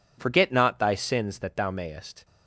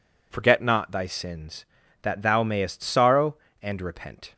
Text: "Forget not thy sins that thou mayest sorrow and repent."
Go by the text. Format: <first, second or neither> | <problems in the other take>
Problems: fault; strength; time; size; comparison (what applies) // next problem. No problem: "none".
second | stops before "sorrow and repent"; at 2.2 s